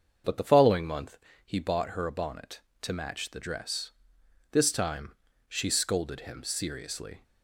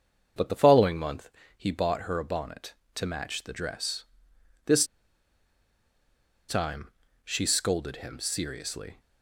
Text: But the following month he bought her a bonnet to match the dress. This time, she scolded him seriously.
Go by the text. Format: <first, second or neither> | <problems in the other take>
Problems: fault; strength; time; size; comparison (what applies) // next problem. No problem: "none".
first | starts louder than the rest; until 1.6 s; 6.5 dB; also in the first // pauses between "month" and "he"; slight; at 1.2 s; 0.28 s long; slight in the first // pauses between "This" and "time"; strong; at 4.8 s; 1.6 s long